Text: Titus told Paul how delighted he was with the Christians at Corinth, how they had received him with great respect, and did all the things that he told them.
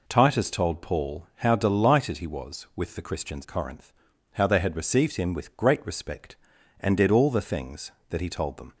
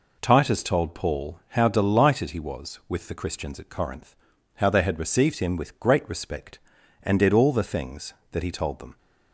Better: second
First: skips "at"; at 3.4 s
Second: none

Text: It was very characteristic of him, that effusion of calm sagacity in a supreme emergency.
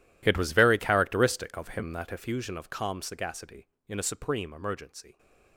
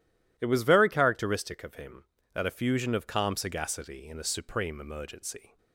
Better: second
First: gets quieter; strong; throughout; 18.5 dB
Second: none

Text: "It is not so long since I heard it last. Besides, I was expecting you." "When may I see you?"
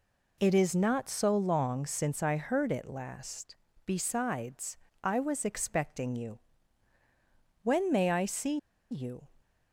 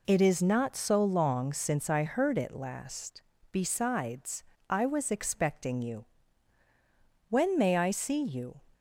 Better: second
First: pauses between "see" and "you"; slight; at 8.5 s; 0.33 s long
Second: none

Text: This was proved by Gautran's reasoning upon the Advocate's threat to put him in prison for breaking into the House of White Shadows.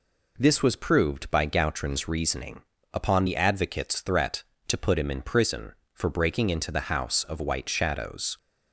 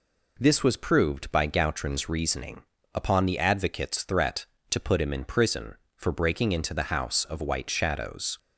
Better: neither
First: pauses between "reasoning" and "upon"; slight; at 2.6 s; 0.32 s long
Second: pauses between "reasoning" and "upon"; slight; at 2.6 s; 0.32 s long

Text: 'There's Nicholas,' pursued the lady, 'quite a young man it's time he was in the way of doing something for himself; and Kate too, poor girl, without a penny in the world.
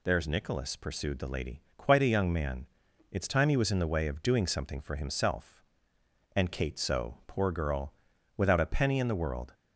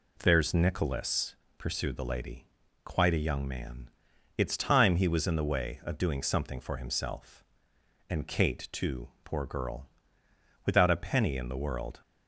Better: second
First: pauses between "man" and "it's"; at 2.6 s; 0.44 s long // says "so" for "too"; at 6.7 s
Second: pauses between "man" and "it's"; noticeable; at 3.8 s; 0.48 s long

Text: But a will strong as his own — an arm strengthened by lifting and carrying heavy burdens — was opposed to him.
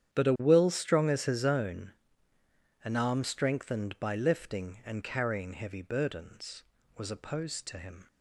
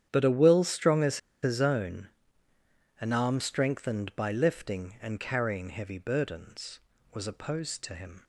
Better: first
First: starts louder than the rest; strong; until 1.2 s; 9.5 dB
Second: starts louder than the rest; strong; until 1.1 s; 9.5 dB // pauses between "as" and "his"; slight; at 1.1 s; 0.24 s long

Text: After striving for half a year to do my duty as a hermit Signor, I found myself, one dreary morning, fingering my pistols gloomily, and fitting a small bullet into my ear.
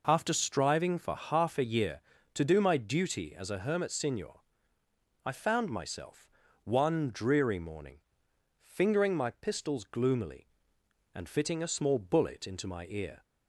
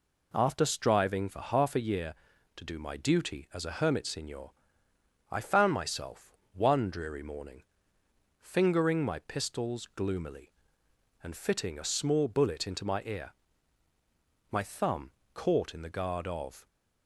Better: first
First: none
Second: goes on to say "My thumb caught in the guard of"; strong; from 14.5 s on; 2.1 s long

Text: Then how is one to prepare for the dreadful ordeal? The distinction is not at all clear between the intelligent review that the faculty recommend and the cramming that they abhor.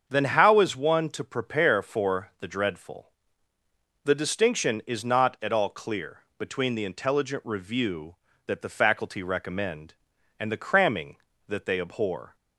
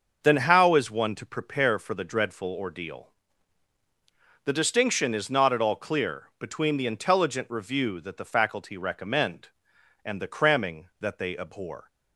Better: second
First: starts louder than the rest; until 1.1 s; 7 dB // skips "ordeal"; at 3.5 s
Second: starts louder than the rest; noticeable; until 1.2 s; 6 dB

